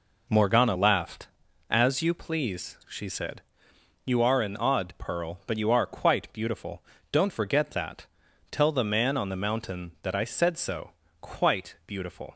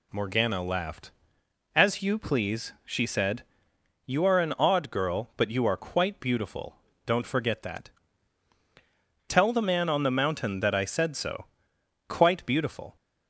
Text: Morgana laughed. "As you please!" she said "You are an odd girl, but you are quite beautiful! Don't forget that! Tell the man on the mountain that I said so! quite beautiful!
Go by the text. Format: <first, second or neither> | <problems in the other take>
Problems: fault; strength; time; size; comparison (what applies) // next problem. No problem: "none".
second | pauses between "said" and "You"; noticeable; at 3.4 s; 0.62 s long; noticeable in the second // says "pearl" for "girl"; at 4.9 s